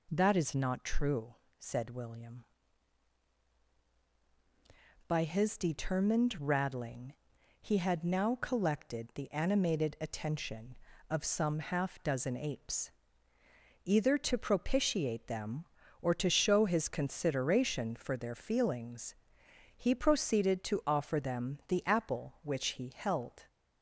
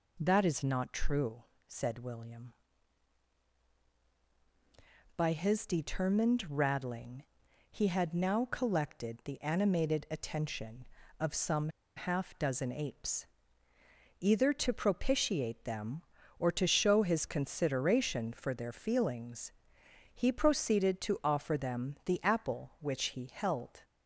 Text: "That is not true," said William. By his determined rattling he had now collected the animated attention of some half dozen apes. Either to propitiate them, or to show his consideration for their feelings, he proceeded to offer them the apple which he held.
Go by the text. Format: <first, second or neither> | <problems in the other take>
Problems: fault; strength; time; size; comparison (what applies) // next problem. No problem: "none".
first | pauses between "rattling" and "he"; noticeable; at 7.2 s; 0.46 s long; noticeable in the first // pauses between "some" and "half"; slight; at 11.6 s; 0.28 s long